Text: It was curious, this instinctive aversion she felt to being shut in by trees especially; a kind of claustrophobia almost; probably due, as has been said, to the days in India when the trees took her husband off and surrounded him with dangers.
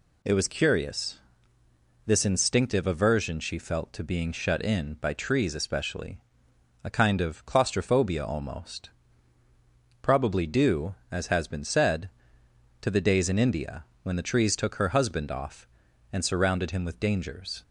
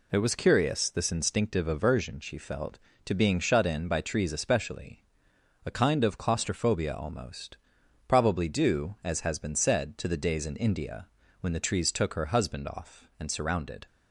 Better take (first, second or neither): first